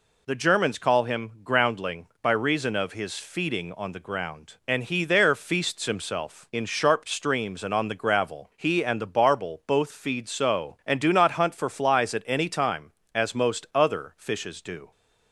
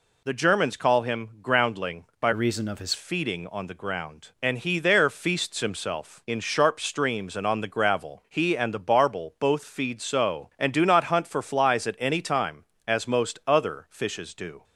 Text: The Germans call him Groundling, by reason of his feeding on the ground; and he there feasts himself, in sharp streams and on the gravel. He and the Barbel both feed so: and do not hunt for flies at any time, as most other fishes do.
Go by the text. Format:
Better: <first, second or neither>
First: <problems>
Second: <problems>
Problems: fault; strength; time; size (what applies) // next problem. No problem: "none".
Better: first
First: none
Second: changes voice from "reason" to "his"; from 2.3 to 2.9 s; 0.6 s long